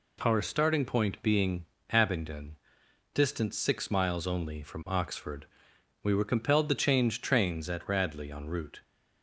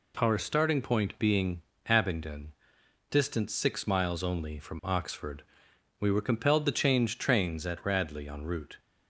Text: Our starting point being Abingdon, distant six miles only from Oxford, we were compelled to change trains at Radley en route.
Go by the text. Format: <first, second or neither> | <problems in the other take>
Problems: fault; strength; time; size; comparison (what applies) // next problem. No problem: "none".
neither | pauses between "being" and "Abingdon"; slight; the same in both